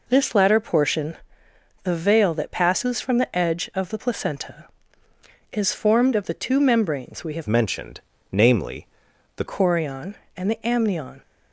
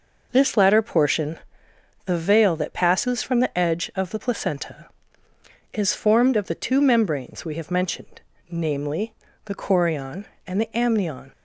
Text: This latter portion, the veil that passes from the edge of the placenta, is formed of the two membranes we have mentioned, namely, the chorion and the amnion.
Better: second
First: changes voice from "mentioned" to "the"; from 7.4 to 9.4 s; 2.0 s long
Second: none

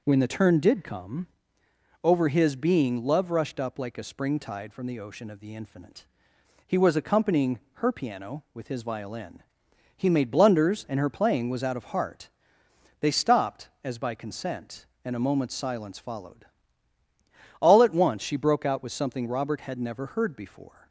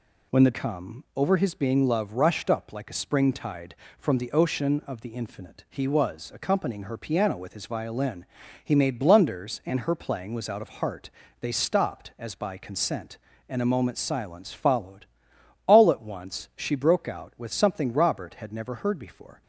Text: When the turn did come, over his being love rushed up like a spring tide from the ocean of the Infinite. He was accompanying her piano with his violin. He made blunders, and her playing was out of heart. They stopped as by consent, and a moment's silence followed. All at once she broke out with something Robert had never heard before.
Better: first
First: none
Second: skips "turn did"; at 0.5 s

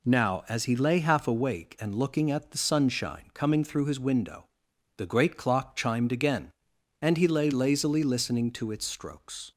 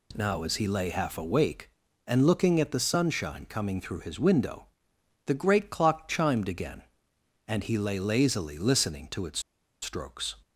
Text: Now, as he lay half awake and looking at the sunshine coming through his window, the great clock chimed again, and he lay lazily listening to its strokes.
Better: first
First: none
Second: pauses between "its" and "strokes"; at 9.3 s; 0.42 s long

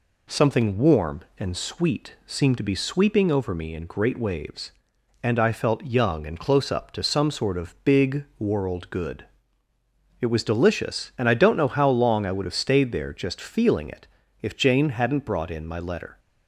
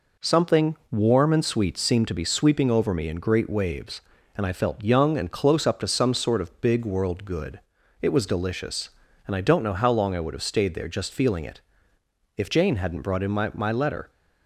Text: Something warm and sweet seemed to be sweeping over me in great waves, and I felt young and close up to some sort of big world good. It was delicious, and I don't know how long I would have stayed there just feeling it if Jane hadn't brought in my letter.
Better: first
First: pauses between "it" and "if"; slight; at 14.0 s; 0.36 s long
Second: pauses between "it" and "if"; noticeable; at 11.5 s; 0.76 s long // says "my" twice; at 13.5 s

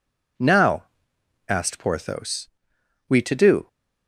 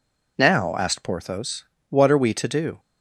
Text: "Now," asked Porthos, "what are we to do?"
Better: second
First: skips "what are"; at 2.7 s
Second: none

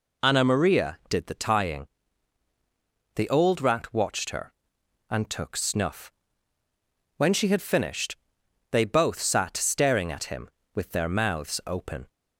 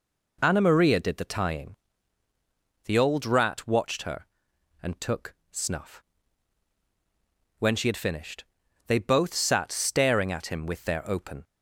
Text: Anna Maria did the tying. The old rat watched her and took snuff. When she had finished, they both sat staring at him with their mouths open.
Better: first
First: none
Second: pauses between "took" and "snuff"; slight; at 5.3 s; 0.18 s long // skips "mouths"; at 11.0 s

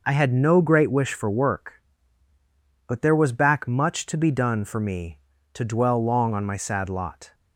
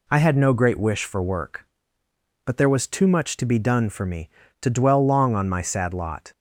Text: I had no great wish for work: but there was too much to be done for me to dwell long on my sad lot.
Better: second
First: says "back" for "too"; at 3.3 s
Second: none

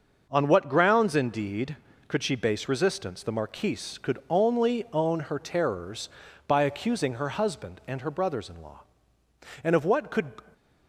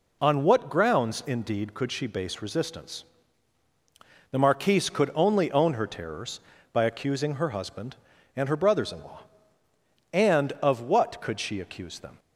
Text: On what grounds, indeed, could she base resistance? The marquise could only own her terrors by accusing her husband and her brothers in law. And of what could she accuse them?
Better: second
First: starts louder than the rest; noticeable; until 1.3 s; 6 dB // stops before "she accuse them"; at 10.5 s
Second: none

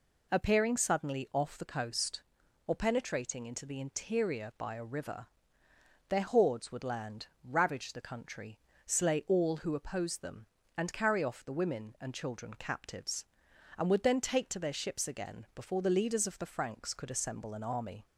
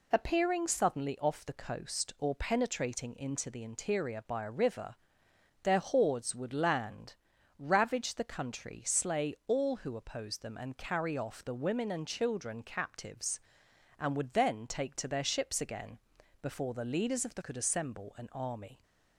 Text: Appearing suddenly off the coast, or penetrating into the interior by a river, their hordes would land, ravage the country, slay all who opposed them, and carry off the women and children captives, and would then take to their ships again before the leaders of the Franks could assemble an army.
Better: first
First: none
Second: pauses between "again" and "before"; at 15.9 s; 0.44 s long // skips "Franks"; at 17.4 s

